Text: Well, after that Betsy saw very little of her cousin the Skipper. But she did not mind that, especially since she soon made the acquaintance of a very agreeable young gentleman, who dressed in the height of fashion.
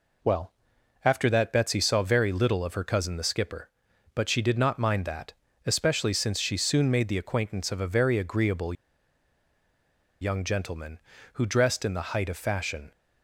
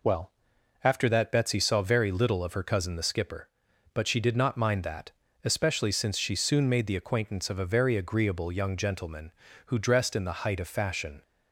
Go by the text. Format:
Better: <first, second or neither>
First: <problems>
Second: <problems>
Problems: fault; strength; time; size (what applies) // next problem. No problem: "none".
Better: second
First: pauses between "agreeable" and "young"; strong; at 8.7 s; 1.4 s long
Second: none